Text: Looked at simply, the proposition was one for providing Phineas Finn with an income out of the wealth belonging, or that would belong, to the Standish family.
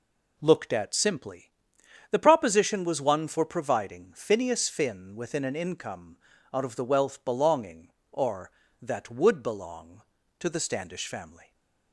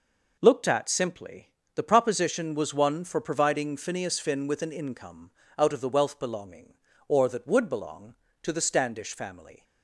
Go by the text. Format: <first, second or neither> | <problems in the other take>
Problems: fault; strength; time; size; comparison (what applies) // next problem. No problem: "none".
second | says "within" for "with"; at 5.1 s // pauses between "income" and "out"; at 6.1 s; 0.38 s long; slight in the second